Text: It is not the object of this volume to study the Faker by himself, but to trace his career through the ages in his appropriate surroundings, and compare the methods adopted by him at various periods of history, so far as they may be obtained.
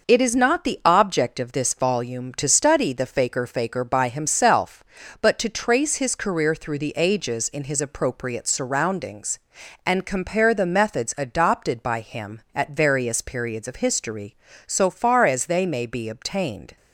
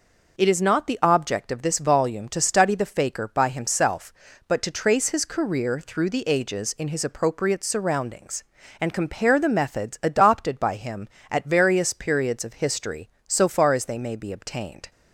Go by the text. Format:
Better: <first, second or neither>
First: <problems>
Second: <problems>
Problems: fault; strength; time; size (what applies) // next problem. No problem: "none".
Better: second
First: says "Faker" twice; at 3.4 s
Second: none